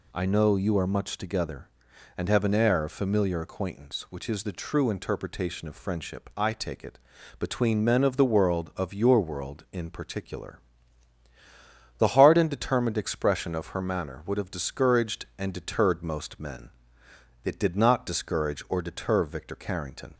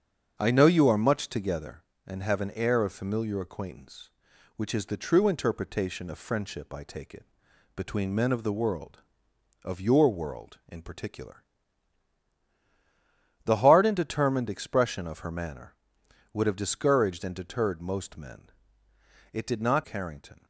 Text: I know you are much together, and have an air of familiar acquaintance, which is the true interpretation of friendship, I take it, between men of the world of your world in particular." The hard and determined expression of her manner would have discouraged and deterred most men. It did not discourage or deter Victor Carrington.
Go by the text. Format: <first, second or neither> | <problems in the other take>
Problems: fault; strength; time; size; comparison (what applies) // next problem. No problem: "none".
first | starts louder than the rest; strong; until 1.3 s; 7.5 dB // skips "discourage or deter Victor"; at 19.8 s